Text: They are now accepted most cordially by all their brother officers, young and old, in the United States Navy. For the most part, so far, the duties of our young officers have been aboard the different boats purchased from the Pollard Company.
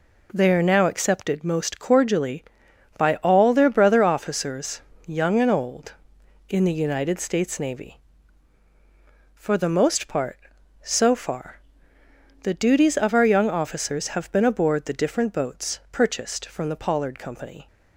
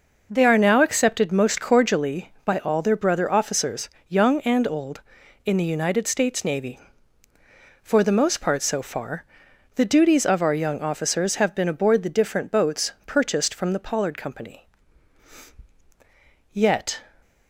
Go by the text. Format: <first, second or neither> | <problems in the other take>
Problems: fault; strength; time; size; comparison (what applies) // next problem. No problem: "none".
first | pauses between "boats" and "purchased"; slight; at 12.9 s; 0.16 s long // goes on to say "Yet"; slight; from 16.5 s on; 0.48 s long